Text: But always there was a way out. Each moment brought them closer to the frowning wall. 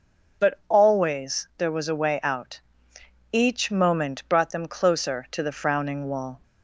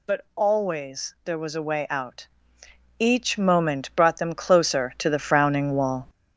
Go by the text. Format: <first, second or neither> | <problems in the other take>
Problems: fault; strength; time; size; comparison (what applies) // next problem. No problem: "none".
first | gets louder; noticeable; throughout; 4.5 dB